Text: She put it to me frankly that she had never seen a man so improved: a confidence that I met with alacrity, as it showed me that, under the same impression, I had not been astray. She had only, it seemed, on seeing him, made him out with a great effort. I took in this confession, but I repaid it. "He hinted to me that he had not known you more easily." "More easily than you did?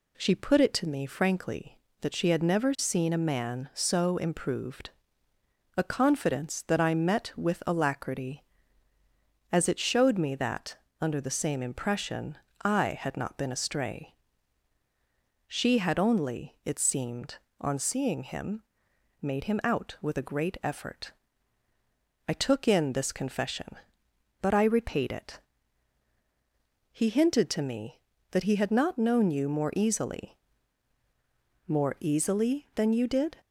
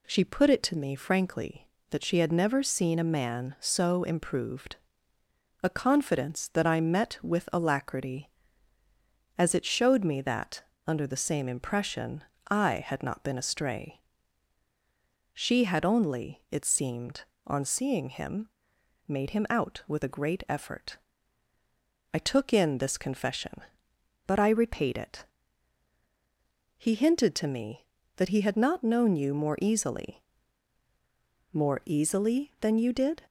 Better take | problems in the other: neither | none

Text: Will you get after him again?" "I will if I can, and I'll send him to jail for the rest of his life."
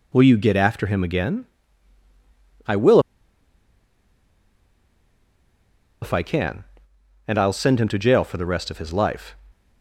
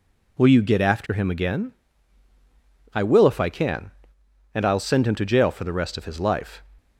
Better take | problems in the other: second | pauses between "will" and "if"; strong; at 2.9 s; 3.0 s long

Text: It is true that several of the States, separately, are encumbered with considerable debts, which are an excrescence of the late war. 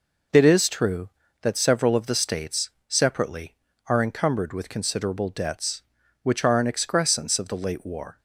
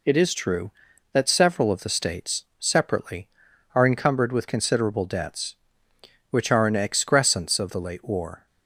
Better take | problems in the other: neither | none

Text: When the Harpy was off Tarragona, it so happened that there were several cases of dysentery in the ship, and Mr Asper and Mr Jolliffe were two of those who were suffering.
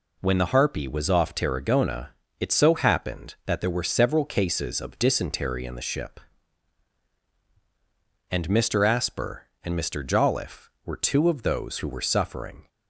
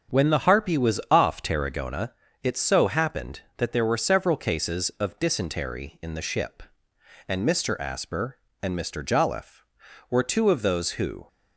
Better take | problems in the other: first | starts louder than the rest; strong; until 1.2 s; 7.5 dB // stops before "were suffering"; at 11.2 s

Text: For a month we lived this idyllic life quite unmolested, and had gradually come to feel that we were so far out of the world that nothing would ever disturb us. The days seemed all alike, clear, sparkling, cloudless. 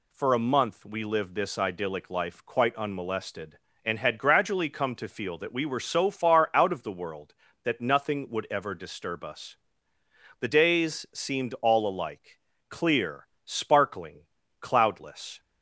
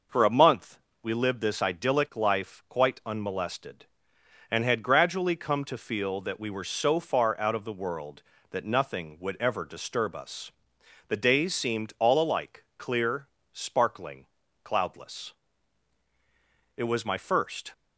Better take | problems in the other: first | pauses between "month" and "we"; slight; at 0.8 s; 0.24 s long // goes on to say "It was my first"; noticeable; from 16.7 s on; 0.98 s long

